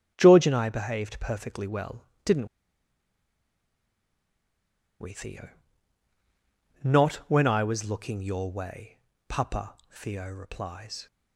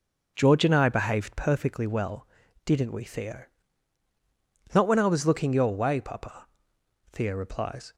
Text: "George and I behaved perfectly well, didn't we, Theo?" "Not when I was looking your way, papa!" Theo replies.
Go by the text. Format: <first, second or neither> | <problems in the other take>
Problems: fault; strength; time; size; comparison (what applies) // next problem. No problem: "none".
second | starts louder than the rest; strong; until 1.1 s; 9.5 dB // pauses between "didn't" and "we"; strong; at 2.4 s; 2.5 s long